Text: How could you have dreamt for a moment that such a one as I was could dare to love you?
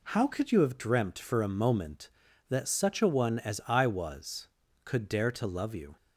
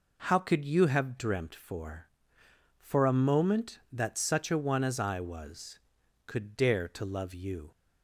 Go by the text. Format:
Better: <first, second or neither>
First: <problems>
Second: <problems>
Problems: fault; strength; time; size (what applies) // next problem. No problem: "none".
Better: first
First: none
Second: says "for" twice; at 2.7 s